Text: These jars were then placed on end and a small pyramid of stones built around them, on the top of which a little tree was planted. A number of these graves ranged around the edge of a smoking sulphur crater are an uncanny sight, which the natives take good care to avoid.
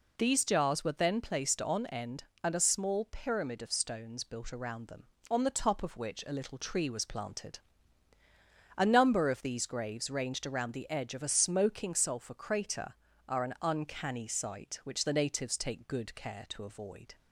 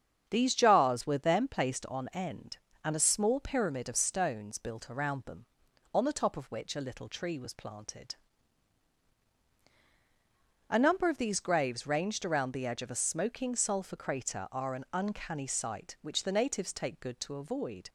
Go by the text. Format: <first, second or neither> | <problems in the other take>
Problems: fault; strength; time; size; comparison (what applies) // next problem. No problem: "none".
first | starts louder than the rest; strong; until 1.2 s; 7.5 dB // skips "care"; at 17.2 s